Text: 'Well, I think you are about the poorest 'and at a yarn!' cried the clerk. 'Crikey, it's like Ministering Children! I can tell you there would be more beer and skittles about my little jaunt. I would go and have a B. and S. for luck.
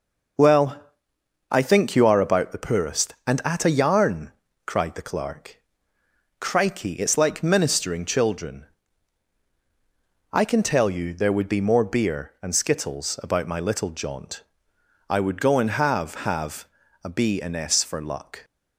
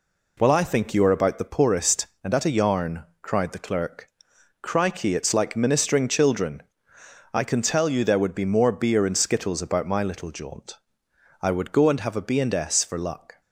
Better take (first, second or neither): second